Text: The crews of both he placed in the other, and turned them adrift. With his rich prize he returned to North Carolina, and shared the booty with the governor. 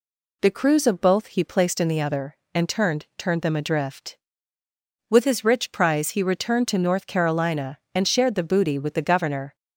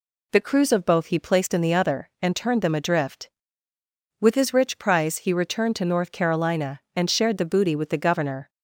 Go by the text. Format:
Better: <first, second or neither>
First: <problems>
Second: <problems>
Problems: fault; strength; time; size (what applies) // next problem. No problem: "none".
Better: second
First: says "turned" twice; at 3.1 s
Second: none